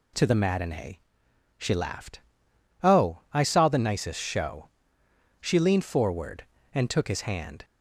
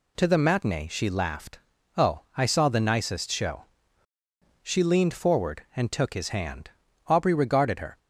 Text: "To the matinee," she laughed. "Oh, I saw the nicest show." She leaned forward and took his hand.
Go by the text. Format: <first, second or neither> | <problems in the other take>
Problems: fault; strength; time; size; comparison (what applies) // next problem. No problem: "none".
first | goes on to say "Aubrey regarded her"; noticeable; from 7.0 s on; 0.92 s long